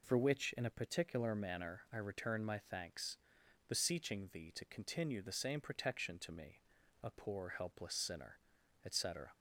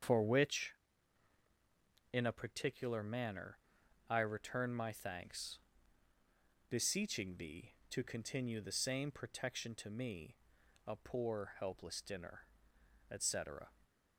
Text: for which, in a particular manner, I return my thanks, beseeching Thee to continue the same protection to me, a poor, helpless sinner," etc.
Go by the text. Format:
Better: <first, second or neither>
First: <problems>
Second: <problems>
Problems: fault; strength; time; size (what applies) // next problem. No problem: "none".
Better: first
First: none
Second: starts louder than the rest; strong; until 2.4 s; 7 dB // says "dinner" for "sinner"; at 12.0 s